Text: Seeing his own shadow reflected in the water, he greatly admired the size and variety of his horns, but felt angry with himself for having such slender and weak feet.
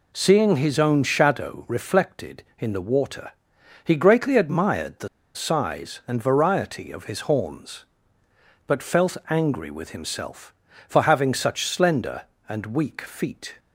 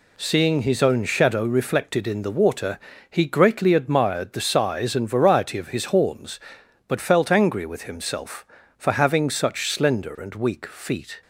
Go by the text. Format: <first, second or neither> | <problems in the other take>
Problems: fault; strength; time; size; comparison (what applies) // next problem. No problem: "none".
second | pauses between "the" and "size"; slight; at 5.0 s; 0.26 s long